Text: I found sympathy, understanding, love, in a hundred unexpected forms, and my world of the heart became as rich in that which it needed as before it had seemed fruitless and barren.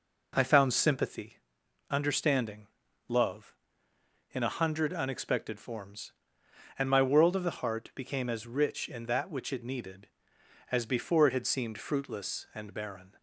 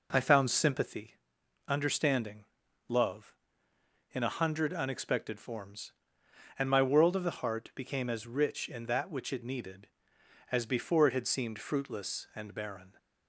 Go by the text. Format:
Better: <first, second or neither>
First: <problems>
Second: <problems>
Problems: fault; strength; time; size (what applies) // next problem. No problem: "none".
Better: neither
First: none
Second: none